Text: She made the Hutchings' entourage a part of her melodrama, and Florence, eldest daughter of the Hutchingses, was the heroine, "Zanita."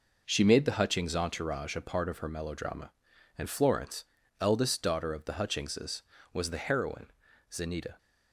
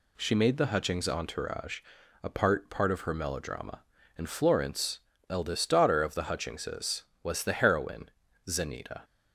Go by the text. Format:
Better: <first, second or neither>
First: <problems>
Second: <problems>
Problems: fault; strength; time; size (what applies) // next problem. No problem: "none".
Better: first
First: none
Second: pauses between "entourage" and "a"; at 1.8 s; 0.42 s long // says "part" twice; at 2.6 s